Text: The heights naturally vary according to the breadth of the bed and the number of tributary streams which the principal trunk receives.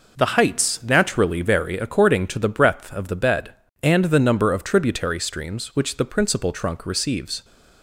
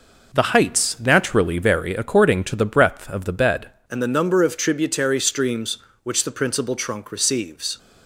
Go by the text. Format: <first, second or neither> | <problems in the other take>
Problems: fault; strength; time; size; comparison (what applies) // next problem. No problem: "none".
first | changes voice at "and"; from 3.8 s on; 3.9 s long